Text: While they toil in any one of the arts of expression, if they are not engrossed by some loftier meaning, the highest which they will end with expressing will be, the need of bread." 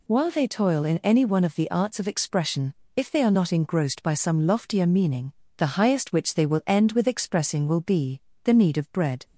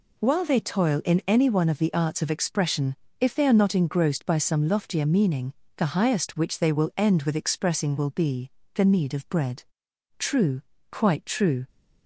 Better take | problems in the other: first | goes on to say "True quite true"; from 10.1 s on; 1.5 s long

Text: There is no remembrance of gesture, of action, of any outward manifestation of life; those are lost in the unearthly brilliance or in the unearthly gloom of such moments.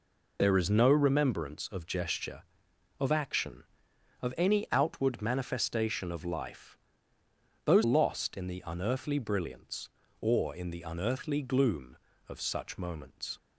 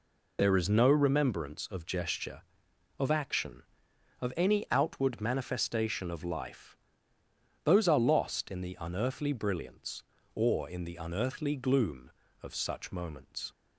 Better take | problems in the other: second | skips "are"; at 7.8 s

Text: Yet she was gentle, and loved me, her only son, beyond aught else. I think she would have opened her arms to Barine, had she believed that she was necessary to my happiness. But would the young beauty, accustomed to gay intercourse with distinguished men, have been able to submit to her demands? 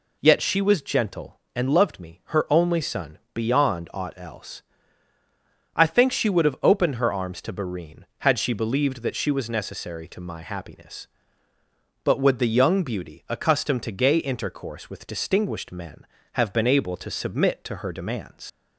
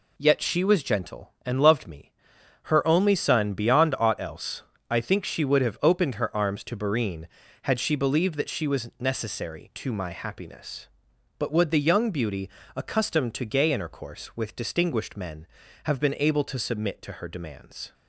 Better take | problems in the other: second | leaves "demands" unfinished; at 18.4 s; 75 ms

